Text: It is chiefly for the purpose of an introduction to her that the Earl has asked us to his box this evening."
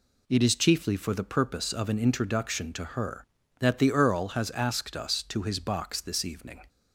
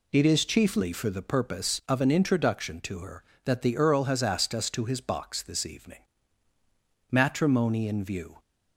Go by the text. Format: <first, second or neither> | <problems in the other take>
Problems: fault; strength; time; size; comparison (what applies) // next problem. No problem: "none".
first | goes on to say "Matrimony in view"; noticeable; from 7.1 s on; 1.2 s long